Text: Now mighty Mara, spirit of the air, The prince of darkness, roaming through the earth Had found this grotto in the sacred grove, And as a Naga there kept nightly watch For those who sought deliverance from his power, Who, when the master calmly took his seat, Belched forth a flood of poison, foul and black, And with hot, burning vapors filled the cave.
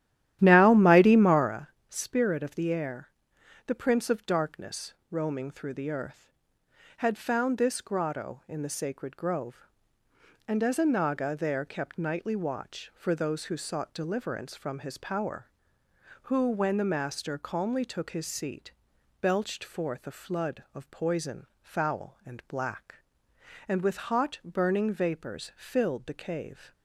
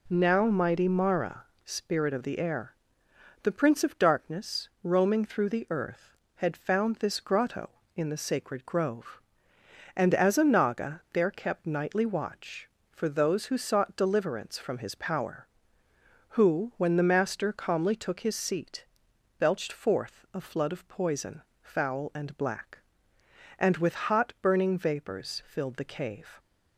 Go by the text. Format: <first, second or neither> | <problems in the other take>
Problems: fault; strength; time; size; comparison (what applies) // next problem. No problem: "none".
second | starts louder than the rest; strong; until 1.6 s; 12.5 dB